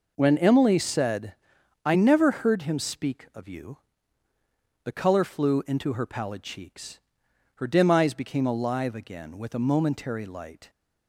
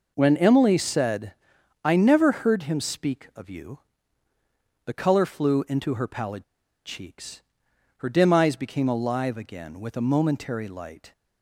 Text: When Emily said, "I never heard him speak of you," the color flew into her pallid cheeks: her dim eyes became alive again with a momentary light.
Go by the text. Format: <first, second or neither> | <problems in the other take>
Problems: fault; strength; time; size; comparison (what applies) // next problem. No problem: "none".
first | pauses between "pallid" and "cheeks"; at 6.4 s; 0.41 s long